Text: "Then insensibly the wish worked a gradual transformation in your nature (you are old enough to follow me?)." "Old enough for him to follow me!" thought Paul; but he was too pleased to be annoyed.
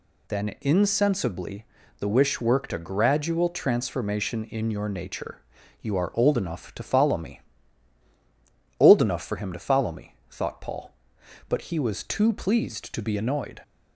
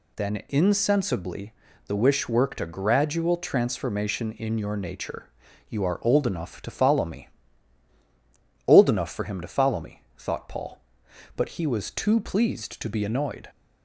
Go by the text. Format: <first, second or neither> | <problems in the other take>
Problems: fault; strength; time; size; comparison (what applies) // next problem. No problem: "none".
neither | pauses between "insensibly" and "the"; slight; the same in both